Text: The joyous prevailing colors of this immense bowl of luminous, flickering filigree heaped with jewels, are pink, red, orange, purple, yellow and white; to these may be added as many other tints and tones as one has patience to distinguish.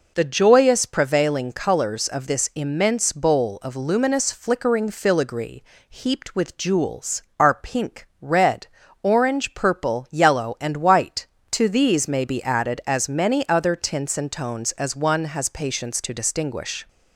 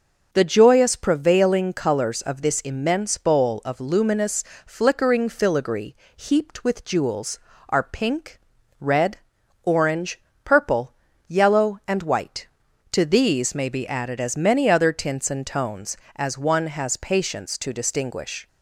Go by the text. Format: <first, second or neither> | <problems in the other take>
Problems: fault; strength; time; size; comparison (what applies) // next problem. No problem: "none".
neither | pauses between "filigree" and "heaped"; slight; the same in both